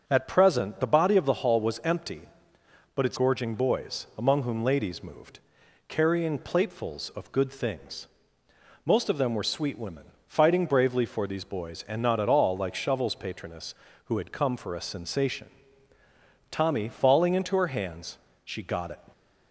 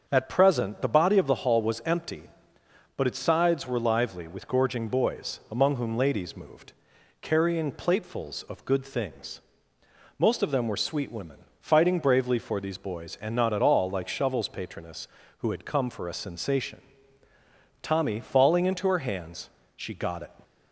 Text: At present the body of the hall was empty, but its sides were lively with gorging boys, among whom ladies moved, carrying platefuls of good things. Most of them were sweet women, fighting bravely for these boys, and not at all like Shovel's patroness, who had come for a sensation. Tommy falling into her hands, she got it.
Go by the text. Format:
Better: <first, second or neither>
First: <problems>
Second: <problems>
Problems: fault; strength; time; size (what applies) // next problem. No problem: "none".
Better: second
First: starts louder than the rest; until 1.0 s; 7 dB // skips "sides were lively with"; at 3.1 s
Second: starts louder than the rest; until 1.0 s; 7 dB